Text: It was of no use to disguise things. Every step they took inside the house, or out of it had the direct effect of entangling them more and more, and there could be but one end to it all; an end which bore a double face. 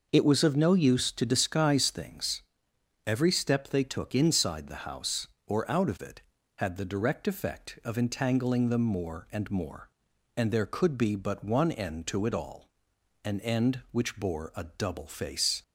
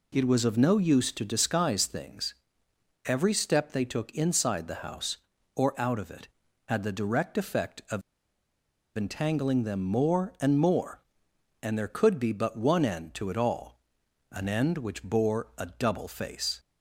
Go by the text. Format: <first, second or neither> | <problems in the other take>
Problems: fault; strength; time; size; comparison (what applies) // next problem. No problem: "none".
first | pauses between "of" and "entangling"; noticeable; at 8.0 s; 0.95 s long